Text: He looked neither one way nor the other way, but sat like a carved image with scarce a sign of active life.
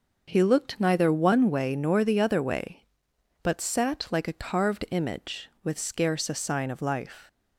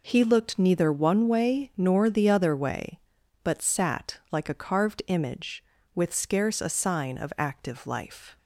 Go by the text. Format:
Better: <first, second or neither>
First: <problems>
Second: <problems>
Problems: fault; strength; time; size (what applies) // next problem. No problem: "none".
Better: second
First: skips "active"; at 6.8 s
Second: none